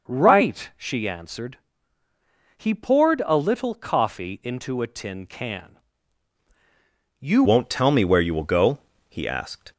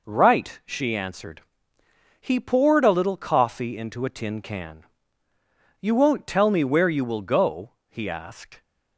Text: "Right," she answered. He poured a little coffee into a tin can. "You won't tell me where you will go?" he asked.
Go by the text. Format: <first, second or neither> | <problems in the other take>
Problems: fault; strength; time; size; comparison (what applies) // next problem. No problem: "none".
second | changes voice at "won't"; from 7.4 s on; 2.3 s long